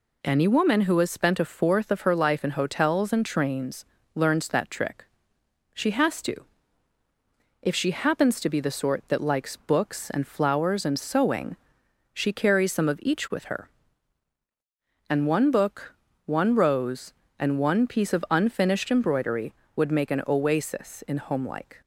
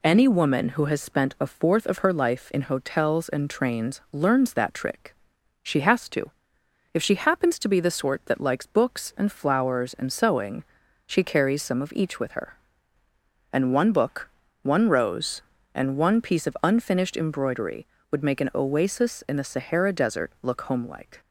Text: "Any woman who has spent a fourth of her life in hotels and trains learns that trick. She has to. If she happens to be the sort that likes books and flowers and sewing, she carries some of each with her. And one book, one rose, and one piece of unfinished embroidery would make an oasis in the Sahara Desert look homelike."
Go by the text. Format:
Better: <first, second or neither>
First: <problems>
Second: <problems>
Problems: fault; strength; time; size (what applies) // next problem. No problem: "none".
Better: second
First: pauses between "trains" and "learns"; slight; at 3.8 s; 0.30 s long // skips "the Sahara Desert look"; at 21.1 s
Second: none